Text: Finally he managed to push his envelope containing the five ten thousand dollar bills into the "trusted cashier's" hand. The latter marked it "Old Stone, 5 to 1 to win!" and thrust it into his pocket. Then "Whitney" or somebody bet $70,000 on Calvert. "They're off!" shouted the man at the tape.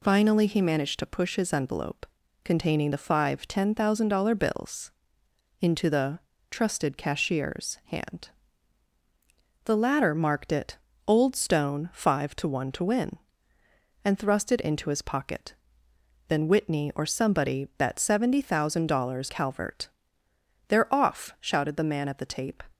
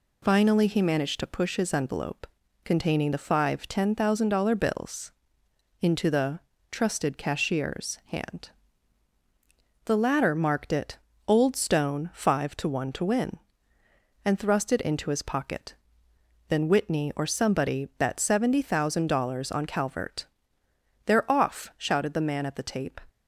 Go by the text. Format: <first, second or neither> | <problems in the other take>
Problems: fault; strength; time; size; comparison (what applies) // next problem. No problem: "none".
second | pauses between "envelope" and "containing"; at 2.0 s; 0.38 s long; also in the second // pauses between "bills" and "into"; noticeable; at 4.9 s; 0.70 s long; noticeable in the second // pauses between "the" and "trusted"; slight; at 6.1 s; 0.32 s long; slight in the second // pauses between "it" and "Old"; slight; at 10.7 s; 0.30 s long; slight in the second // skips "on"; at 19.2 s